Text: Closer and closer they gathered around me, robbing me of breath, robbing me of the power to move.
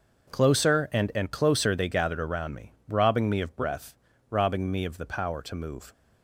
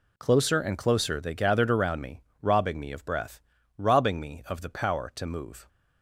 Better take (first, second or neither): second